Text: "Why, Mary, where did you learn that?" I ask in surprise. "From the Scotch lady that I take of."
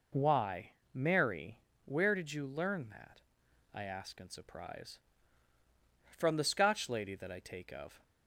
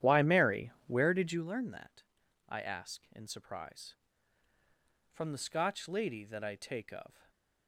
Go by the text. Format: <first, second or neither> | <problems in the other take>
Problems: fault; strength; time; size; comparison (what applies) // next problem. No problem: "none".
first | starts louder than the rest; strong; until 1.5 s; 11 dB // stays silent after the last word; slight; from 7.1 s on; 0.5 s long